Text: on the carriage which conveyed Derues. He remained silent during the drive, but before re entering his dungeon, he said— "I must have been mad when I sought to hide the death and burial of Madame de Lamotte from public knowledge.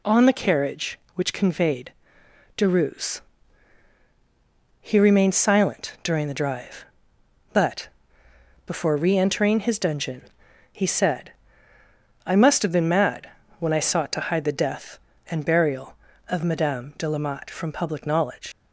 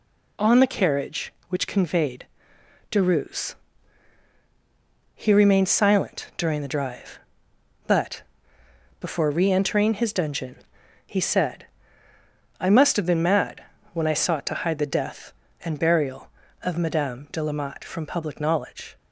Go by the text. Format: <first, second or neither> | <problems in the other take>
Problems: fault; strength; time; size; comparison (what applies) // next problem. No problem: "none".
second | pauses between "conveyed" and "Derues"; noticeable; at 1.9 s; 0.64 s long; noticeable in the second // pauses between "but" and "before"; noticeable; at 7.8 s; 0.76 s long; noticeable in the second // pauses between "mad" and "when"; slight; at 13.2 s; 0.30 s long; slight in the second // leaves "knowledge" unfinished; at 18.5 s; 115 ms